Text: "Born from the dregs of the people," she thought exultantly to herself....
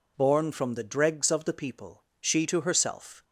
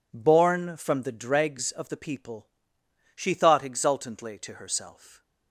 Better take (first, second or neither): second